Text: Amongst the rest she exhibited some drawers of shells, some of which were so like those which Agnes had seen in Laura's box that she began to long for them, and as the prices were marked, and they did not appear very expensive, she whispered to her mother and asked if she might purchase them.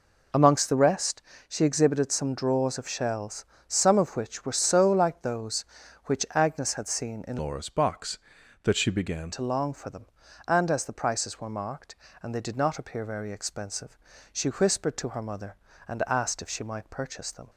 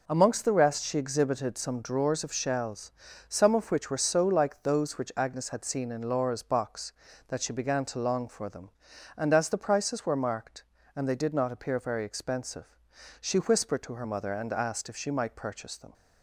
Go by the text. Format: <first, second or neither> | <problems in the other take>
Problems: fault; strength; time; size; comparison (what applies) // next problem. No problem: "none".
second | pauses between "rest" and "she"; slight; at 1.2 s; 0.26 s long // changes voice from "Laura's" to "began"; from 7.3 to 9.3 s; 2.0 s long